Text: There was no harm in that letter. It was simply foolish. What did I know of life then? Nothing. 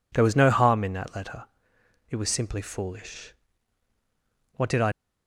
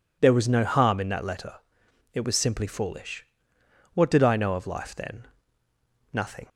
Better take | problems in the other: second | stops before "know of life then Nothing"; at 4.9 s

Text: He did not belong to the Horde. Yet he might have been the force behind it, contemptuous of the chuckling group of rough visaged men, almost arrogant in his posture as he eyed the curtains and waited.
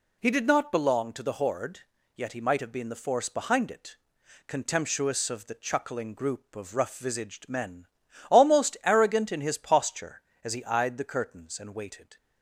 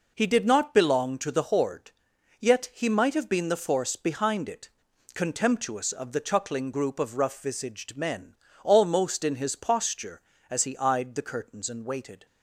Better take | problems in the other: first | skips "arrogant"; at 9.2 s

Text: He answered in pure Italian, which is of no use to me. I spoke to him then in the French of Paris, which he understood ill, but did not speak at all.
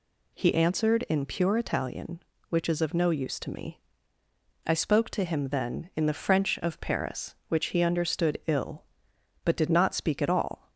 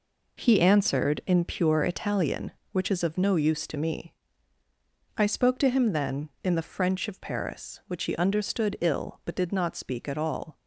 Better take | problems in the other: neither | none

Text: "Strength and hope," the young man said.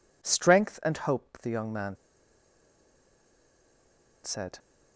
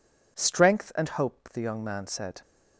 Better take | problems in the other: second | pauses between "man" and "said"; strong; at 1.9 s; 2.2 s long

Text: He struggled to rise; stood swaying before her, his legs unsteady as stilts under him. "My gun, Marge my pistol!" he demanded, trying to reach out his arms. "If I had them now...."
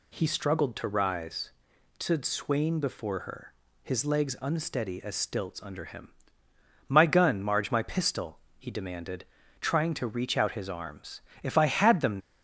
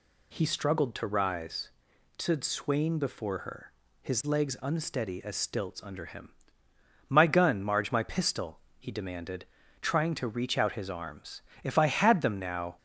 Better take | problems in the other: second | stops before "now"; at 12.2 s

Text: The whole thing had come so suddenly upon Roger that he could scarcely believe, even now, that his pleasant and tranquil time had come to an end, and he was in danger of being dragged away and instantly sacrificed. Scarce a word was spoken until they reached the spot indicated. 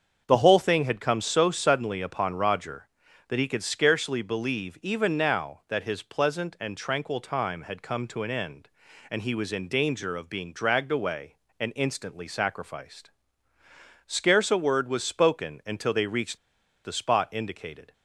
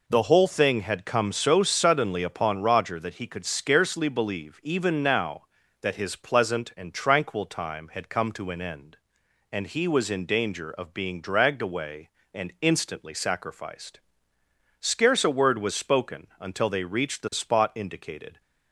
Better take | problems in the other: second | starts louder than the rest; until 1.2 s; 7 dB // pauses between "reached" and "the"; noticeable; at 16.3 s; 0.46 s long

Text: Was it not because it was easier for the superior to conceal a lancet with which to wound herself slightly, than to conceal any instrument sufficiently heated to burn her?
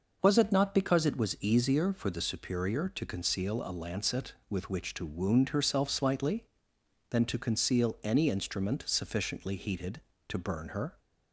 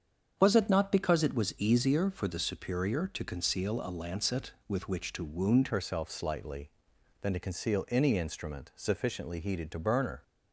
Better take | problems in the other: first | starts louder than the rest; strong; until 1.3 s; 7.5 dB // changes voice at "herself"; from 5.6 s on; 4.6 s long

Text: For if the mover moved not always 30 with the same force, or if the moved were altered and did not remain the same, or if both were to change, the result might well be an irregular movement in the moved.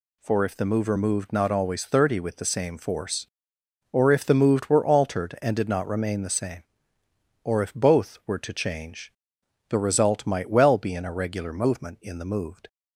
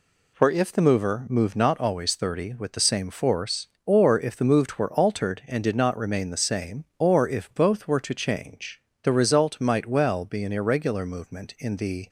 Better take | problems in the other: first | stops before "moved"; at 12.0 s

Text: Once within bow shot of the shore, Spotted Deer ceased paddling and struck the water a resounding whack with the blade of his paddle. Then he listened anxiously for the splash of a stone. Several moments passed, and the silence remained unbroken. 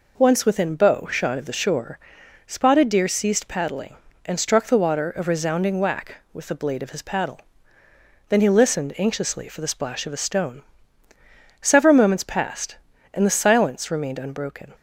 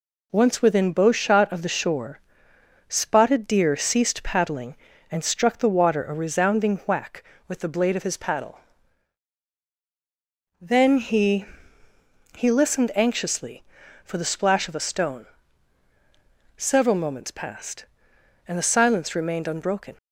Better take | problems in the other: first | says "he" twice; at 12.3 s

